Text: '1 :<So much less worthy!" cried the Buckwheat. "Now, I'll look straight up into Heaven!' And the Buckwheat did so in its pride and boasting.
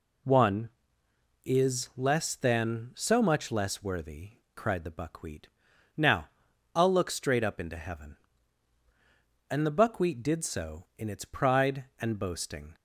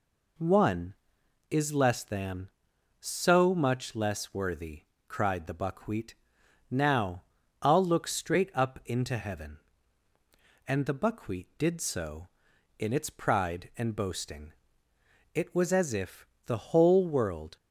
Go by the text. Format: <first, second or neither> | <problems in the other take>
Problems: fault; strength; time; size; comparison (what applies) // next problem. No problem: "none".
first | goes on to say "It was as if the whole world"; strong; from 15.3 s on; 2.2 s long